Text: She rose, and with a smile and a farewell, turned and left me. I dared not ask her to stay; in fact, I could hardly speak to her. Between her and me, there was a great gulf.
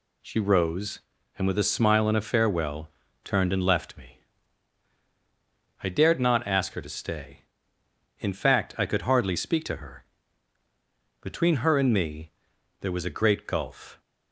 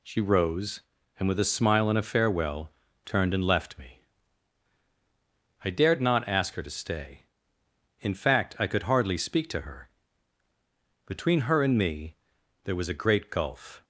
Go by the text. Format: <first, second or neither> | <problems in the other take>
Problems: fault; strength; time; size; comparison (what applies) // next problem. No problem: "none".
neither | none